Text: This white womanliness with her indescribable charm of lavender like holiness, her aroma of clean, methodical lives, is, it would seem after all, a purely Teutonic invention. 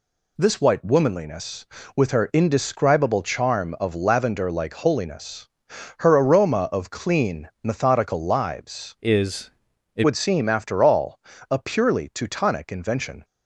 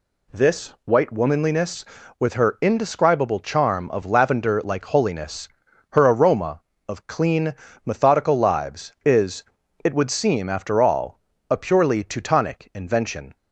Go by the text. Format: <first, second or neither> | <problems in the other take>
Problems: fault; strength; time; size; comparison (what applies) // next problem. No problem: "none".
second | changes voice from "is" to "it"; from 9.0 to 10.0 s; 1.0 s long